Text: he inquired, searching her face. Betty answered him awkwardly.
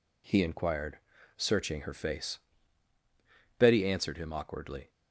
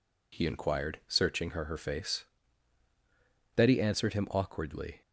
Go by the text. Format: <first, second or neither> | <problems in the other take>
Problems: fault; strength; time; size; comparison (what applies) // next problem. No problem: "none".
first | says "her" twice; at 1.6 s